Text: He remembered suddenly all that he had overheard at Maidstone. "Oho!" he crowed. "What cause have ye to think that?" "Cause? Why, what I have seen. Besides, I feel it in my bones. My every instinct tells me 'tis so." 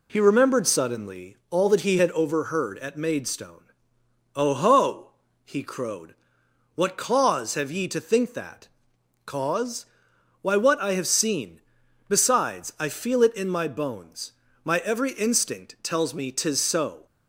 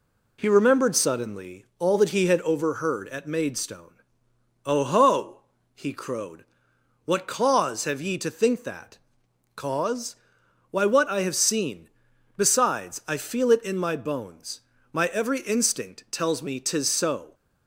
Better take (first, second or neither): neither